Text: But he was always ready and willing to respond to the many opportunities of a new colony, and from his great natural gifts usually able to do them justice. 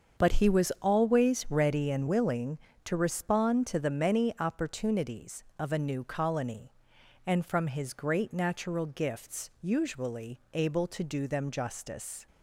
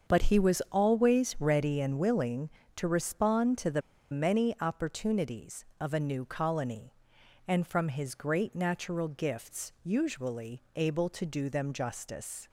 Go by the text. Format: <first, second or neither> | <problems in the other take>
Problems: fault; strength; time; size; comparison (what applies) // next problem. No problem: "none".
first | starts louder than the rest; until 1.1 s; 7 dB; also in the first // pauses between "the" and "many"; slight; at 3.8 s; 0.30 s long